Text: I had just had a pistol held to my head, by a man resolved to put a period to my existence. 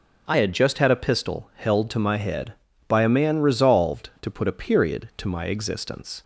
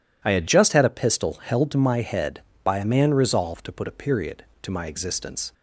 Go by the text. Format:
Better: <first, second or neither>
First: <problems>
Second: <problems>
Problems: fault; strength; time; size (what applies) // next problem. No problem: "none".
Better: first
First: none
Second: changes voice at "just"; from 0.4 s on; 5.1 s long